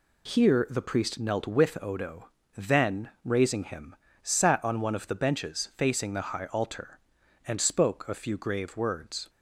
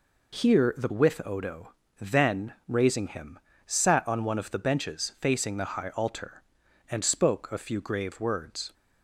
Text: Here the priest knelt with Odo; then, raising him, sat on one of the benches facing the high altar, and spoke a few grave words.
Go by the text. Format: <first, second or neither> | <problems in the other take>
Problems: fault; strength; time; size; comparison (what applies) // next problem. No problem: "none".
first | skips "priest knelt"; at 0.8 s